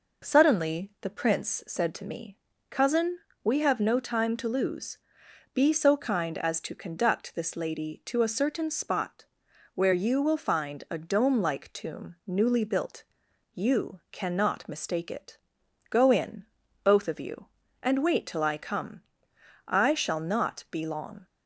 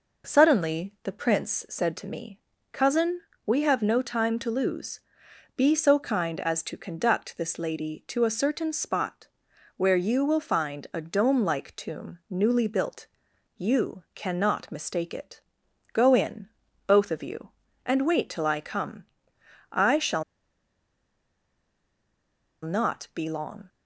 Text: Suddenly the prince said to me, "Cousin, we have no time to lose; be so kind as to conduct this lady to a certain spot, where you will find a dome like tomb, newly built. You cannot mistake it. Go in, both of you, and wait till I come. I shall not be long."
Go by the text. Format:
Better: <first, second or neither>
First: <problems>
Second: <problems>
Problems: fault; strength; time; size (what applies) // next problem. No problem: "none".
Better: first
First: none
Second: pauses between "shall" and "not"; strong; at 20.2 s; 2.4 s long